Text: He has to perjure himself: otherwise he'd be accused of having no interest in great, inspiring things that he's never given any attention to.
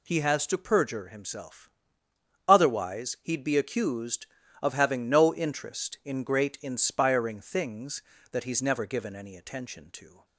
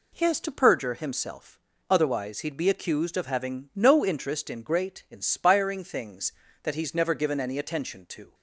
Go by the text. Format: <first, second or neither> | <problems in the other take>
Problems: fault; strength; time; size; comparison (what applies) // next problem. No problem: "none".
neither | none